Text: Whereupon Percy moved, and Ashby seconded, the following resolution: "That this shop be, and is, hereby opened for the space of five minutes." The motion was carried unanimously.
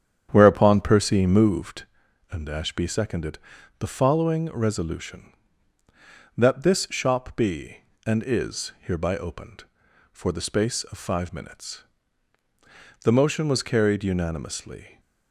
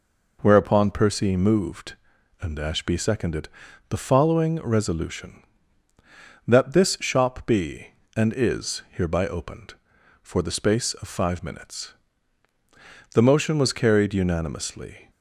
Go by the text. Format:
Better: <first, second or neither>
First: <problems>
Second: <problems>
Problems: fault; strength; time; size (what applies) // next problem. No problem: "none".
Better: second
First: starts louder than the rest; strong; until 1.9 s; 8.5 dB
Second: none